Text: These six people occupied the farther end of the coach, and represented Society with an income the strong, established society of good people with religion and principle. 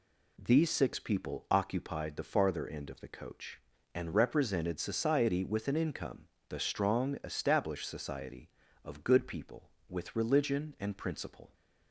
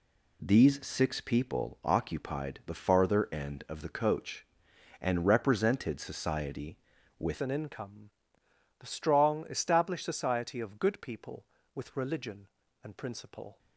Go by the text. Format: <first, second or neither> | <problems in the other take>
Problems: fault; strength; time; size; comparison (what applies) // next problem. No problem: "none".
first | changes voice at "an"; from 7.3 s on; 6.2 s long // pauses between "income" and "the"; noticeable; at 8.0 s; 0.70 s long; slight in the first